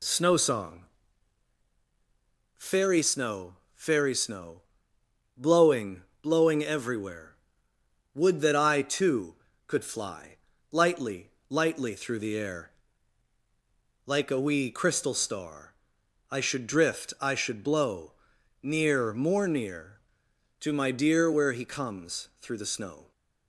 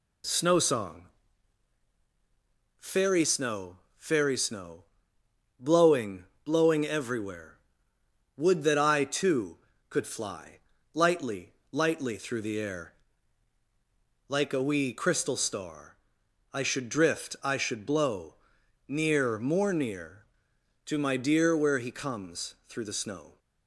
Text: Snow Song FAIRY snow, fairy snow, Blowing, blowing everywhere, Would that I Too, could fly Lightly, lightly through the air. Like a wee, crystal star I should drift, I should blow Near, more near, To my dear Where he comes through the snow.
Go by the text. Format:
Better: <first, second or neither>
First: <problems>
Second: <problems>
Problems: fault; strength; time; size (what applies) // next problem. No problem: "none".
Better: neither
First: pauses between "Song" and "FAIRY"; strong; at 0.8 s; 1.7 s long // pauses between "fly" and "Lightly"; slight; at 10.3 s; 0.34 s long // pauses between "star" and "I"; noticeable; at 15.7 s; 0.54 s long // pauses between "blow" and "Near"; noticeable; at 18.1 s; 0.50 s long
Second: pauses between "Song" and "FAIRY"; strong; at 1.0 s; 1.7 s long // pauses between "fly" and "Lightly"; slight; at 10.6 s; 0.34 s long // pauses between "star" and "I"; noticeable; at 15.9 s; 0.54 s long // pauses between "blow" and "Near"; noticeable; at 18.3 s; 0.53 s long